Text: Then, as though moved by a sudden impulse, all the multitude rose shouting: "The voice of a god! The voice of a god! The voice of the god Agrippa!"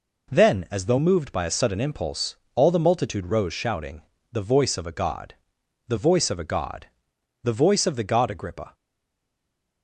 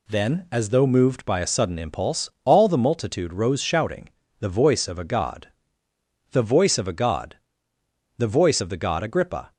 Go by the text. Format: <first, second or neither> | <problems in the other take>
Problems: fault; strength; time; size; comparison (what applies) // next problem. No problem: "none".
second | stays silent after the last word; from 8.7 s on; 1.1 s long